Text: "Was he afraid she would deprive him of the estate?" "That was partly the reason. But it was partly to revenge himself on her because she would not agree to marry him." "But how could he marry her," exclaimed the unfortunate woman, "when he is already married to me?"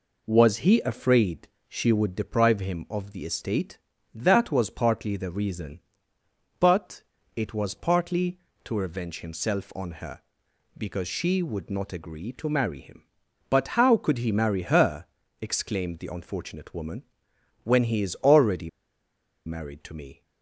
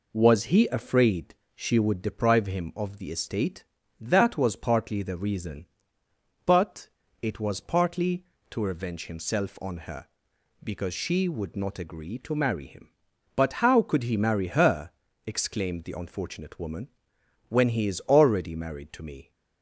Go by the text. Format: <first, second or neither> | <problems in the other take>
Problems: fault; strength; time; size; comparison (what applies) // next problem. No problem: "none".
second | pauses between "afraid" and "she"; slight; at 1.4 s; 0.20 s long; slight in the second // pauses between "But" and "it"; slight; at 7.0 s; 0.32 s long; slight in the second // pauses between "already" and "married"; noticeable; at 18.6 s; 0.77 s long